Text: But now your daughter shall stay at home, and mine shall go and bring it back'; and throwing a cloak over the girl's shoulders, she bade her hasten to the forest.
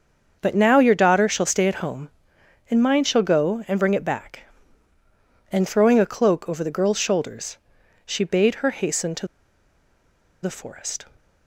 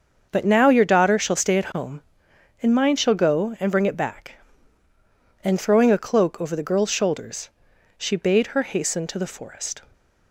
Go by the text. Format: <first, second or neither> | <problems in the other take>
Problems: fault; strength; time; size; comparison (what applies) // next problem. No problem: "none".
second | starts louder than the rest; until 1.4 s; 6.5 dB; also in the second // pauses between "to" and "the"; at 9.2 s; 1.1 s long